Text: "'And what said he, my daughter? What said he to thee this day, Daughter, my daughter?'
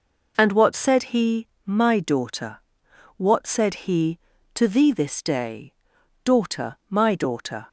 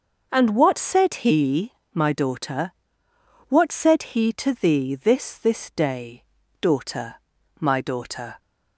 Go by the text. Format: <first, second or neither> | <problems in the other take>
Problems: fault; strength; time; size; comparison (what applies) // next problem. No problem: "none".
first | starts louder than the rest; until 1.3 s; 6 dB // says "this" twice; at 5.3 s